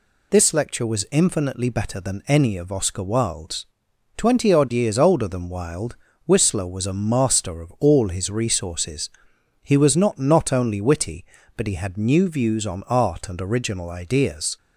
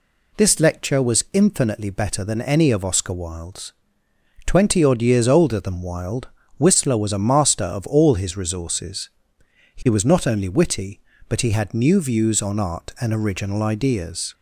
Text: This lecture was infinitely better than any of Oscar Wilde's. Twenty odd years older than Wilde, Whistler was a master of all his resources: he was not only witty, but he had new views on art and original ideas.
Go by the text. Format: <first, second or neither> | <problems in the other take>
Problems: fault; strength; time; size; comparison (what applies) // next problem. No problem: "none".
second | says "not" twice; at 10.1 s